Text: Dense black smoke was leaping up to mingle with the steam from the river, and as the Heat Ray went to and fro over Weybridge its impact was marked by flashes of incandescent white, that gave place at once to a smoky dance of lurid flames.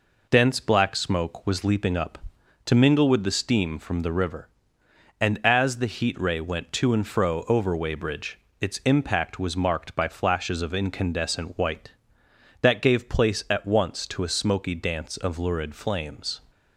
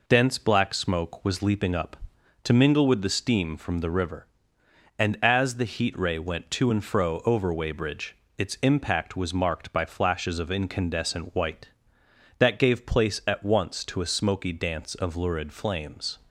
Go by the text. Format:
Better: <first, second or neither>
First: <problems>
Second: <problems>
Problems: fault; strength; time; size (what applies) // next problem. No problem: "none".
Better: neither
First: pauses between "Weybridge" and "its"; slight; at 8.3 s; 0.22 s long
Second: pauses between "Weybridge" and "its"; slight; at 8.1 s; 0.22 s long